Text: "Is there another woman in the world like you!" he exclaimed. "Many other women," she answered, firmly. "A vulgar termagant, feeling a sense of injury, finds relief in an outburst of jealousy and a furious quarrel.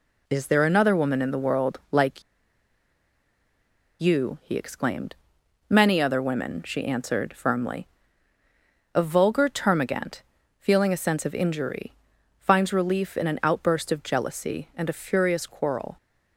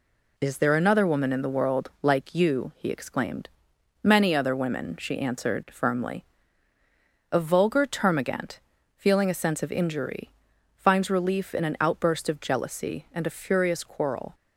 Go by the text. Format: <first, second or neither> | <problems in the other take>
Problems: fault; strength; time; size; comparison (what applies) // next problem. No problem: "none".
second | pauses between "like" and "you"; strong; at 2.2 s; 1.7 s long